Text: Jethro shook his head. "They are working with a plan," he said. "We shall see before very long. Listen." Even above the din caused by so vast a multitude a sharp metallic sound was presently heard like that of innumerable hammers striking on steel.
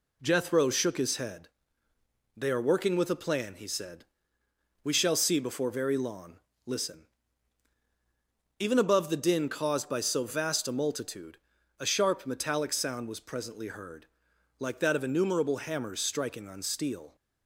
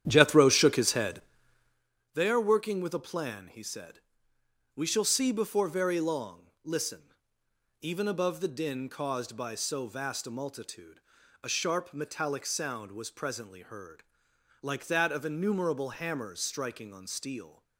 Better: first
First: pauses between "multitude" and "a"; at 11.3 s; 0.44 s long // pauses between "heard" and "like"; noticeable; at 14.0 s; 0.54 s long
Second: starts louder than the rest; strong; until 1.9 s; 10.5 dB // pauses between "multitude" and "a"; at 11.0 s; 0.42 s long // pauses between "heard" and "like"; noticeable; at 14.0 s; 0.58 s long

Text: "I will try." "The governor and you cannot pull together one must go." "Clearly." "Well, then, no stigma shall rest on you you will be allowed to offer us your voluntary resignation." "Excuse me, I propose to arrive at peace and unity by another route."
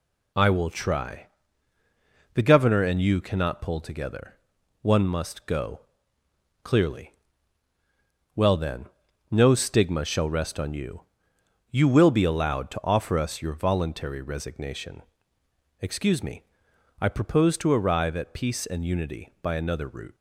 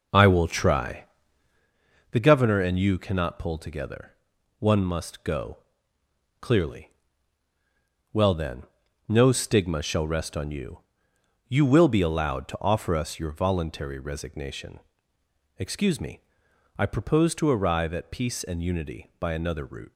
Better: first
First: pauses between "together" and "one"; at 4.3 s; 0.42 s long // pauses between "you" and "you"; noticeable; at 11.0 s; 0.66 s long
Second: starts louder than the rest; noticeable; until 1.7 s; 5 dB // pauses between "together" and "one"; at 4.1 s; 0.42 s long // pauses between "you" and "you"; noticeable; at 10.7 s; 0.66 s long

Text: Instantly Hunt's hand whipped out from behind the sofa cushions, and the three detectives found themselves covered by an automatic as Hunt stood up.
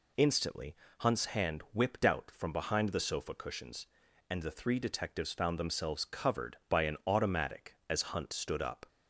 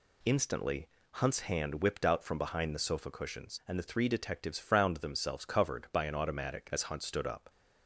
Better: first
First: pauses between "Instantly" and "Hunt's"; slight; at 0.7 s; 0.22 s long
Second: pauses between "Instantly" and "Hunt's"; slight; at 0.8 s; 0.28 s long // says "frowned" for "found"; at 4.5 s

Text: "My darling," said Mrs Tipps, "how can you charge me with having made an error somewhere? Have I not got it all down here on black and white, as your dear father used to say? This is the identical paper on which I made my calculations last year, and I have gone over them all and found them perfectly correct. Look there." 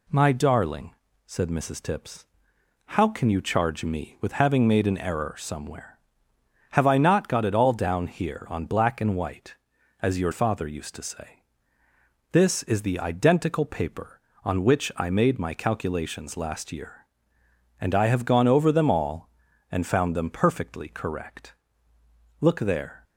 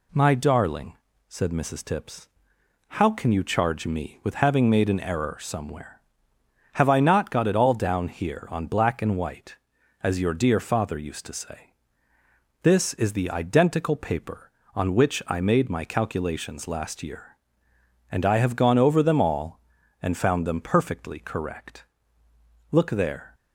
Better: second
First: skips "dear"; at 10.3 s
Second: none

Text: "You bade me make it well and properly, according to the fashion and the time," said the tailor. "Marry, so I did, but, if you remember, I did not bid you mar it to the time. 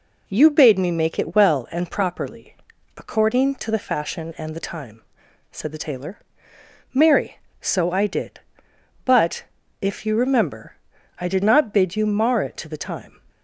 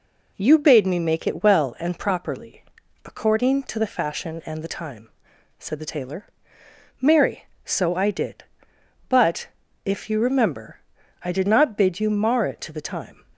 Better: neither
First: none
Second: none

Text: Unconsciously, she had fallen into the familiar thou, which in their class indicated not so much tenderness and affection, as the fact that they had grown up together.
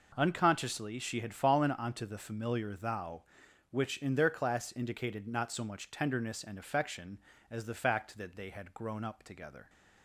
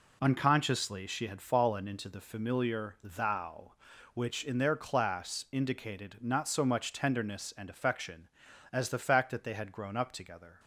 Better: second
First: says "onto" for "into"; at 1.7 s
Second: none

